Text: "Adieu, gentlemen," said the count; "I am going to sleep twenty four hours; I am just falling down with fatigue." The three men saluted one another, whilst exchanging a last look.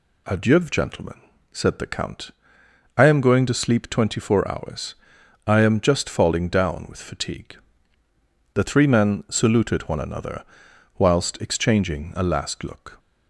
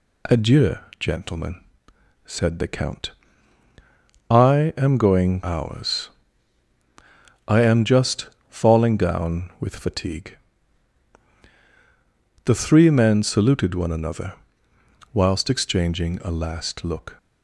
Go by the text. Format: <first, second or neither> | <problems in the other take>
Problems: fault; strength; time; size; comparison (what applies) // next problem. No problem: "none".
first | skips "to sleep twenty four"; at 5.4 s // pauses between "just" and "falling"; slight; at 8.2 s; 0.20 s long